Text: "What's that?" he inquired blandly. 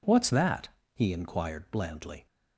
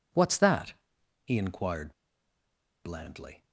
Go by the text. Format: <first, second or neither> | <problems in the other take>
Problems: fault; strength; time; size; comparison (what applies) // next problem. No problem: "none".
first | pauses between "inquired" and "blandly"; noticeable; at 1.9 s; 0.92 s long